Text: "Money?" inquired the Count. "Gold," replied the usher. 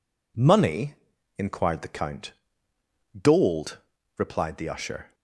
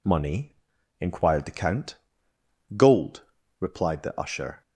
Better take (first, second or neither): neither